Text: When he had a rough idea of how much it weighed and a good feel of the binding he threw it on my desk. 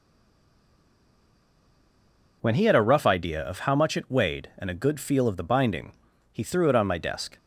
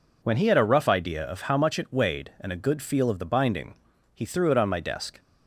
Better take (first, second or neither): second